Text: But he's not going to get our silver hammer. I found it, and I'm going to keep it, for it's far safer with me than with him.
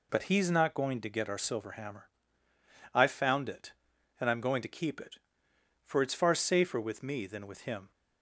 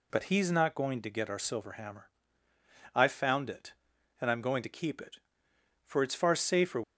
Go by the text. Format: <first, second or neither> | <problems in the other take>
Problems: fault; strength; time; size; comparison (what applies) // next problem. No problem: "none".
first | stops before "with me than with him"; at 6.8 s